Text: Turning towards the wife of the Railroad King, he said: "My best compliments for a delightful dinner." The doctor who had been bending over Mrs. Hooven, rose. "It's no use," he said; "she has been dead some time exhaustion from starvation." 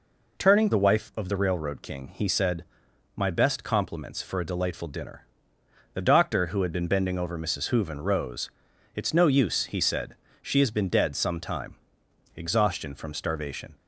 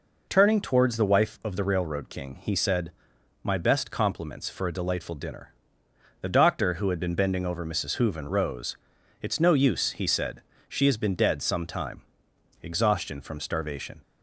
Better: second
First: skips "towards"; at 0.7 s // pauses between "time" and "exhaustion"; noticeable; at 11.7 s; 0.60 s long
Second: pauses between "time" and "exhaustion"; noticeable; at 12.0 s; 0.60 s long

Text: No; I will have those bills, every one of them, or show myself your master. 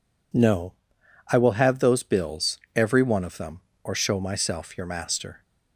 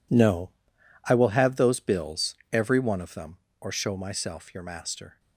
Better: first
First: none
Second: gets quieter; strong; throughout; 15.5 dB

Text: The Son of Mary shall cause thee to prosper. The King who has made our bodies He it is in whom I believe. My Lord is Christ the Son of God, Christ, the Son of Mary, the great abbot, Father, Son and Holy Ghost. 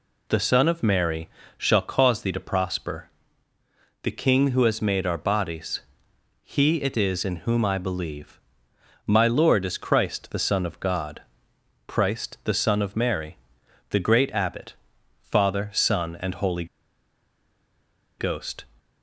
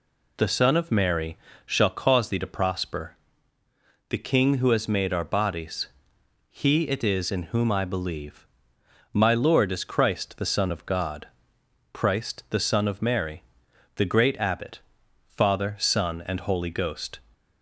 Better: second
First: pauses between "Mary" and "shall"; slight; at 1.2 s; 0.26 s long // pauses between "bodies" and "He"; noticeable; at 5.8 s; 0.62 s long // pauses between "Holy" and "Ghost"; strong; at 16.6 s; 1.5 s long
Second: pauses between "Mary" and "shall"; slight; at 1.3 s; 0.26 s long // pauses between "bodies" and "He"; noticeable; at 5.8 s; 0.62 s long

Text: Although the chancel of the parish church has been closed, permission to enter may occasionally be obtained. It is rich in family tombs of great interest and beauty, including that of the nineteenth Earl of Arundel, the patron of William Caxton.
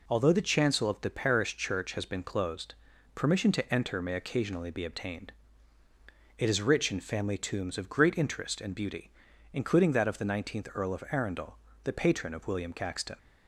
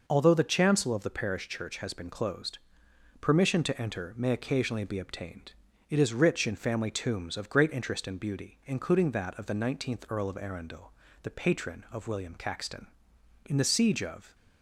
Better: first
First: none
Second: goes on to say "In the siege of"; noticeable; from 13.4 s on; 0.90 s long

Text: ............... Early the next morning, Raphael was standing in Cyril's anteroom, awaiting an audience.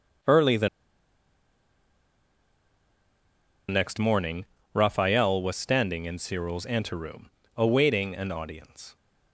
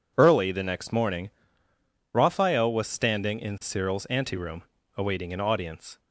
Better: second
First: pauses between "the" and "next"; strong; at 0.6 s; 3.0 s long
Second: none

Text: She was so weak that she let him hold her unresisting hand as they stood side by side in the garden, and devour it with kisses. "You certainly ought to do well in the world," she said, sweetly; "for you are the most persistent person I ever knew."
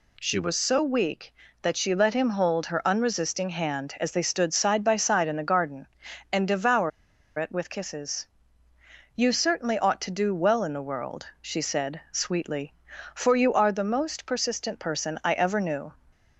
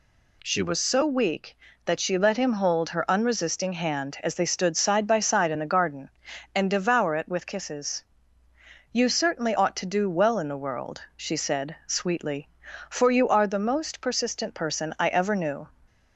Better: second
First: pauses between "devour" and "it"; noticeable; at 6.9 s; 0.48 s long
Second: none

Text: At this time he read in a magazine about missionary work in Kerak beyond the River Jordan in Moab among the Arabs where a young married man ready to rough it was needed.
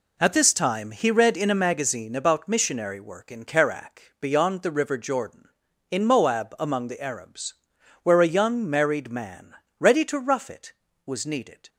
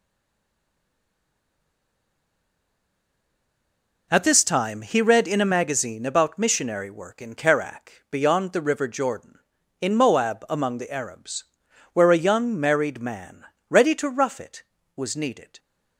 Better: first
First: pauses between "Arabs" and "where"; noticeable; at 7.5 s; 0.50 s long // pauses between "man" and "ready"; slight; at 9.5 s; 0.26 s long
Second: stays silent before the first word; strong; until 4.1 s; 4.1 s long // pauses between "Arabs" and "where"; noticeable; at 11.4 s; 0.50 s long // pauses between "man" and "ready"; slight; at 13.4 s; 0.26 s long

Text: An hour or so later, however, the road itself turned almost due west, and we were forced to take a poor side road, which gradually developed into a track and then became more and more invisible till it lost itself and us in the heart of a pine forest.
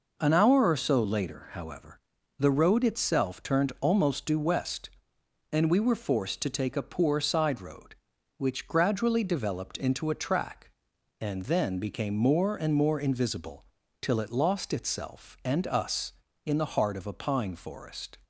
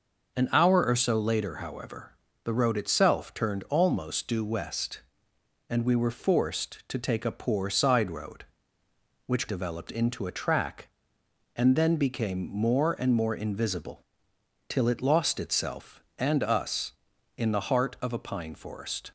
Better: first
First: pauses between "invisible" and "till"; slight; at 13.6 s; 0.34 s long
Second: skips "gradually"; at 9.4 s // pauses between "invisible" and "till"; noticeable; at 14.0 s; 0.68 s long

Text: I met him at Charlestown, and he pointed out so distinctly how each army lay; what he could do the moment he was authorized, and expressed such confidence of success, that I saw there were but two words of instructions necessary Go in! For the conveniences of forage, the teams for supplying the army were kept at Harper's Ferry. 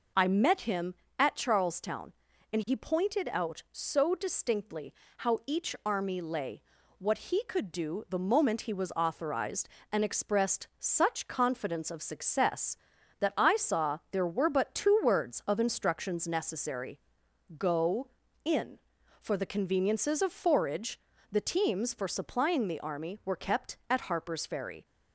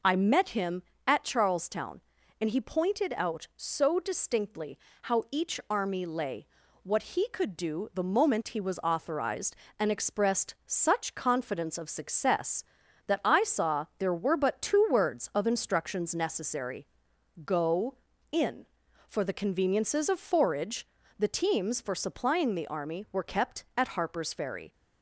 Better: neither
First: pauses between "distinctly" and "how"; slight; at 4.9 s; 0.26 s long // pauses between "necessary" and "Go"; noticeable; at 17.0 s; 0.58 s long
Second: pauses between "distinctly" and "how"; slight; at 4.7 s; 0.26 s long // pauses between "necessary" and "Go"; noticeable; at 16.8 s; 0.58 s long

